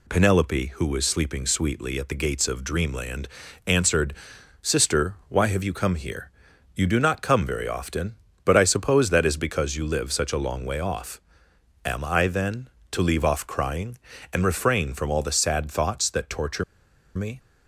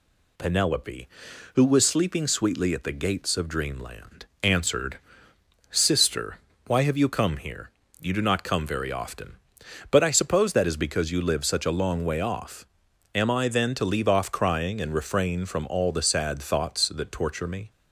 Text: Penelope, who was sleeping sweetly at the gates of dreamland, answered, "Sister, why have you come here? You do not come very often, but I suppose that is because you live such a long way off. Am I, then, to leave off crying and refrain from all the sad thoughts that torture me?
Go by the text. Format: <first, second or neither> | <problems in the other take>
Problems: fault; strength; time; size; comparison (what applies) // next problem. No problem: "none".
second | pauses between "torture" and "me"; noticeable; at 16.6 s; 0.51 s long